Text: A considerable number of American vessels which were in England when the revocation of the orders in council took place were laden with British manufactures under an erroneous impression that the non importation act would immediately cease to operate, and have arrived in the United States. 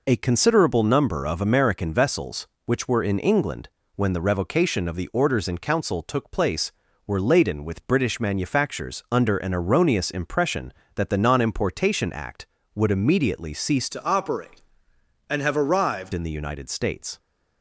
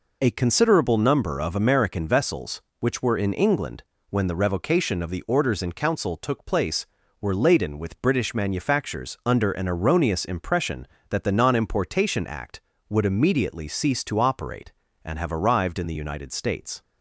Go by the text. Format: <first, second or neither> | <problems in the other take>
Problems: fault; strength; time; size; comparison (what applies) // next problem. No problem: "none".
second | pauses between "England" and "when"; slight; at 3.6 s; 0.26 s long; slight in the second // changes voice from "to" to "arrived"; from 13.9 to 16.1 s; 2.2 s long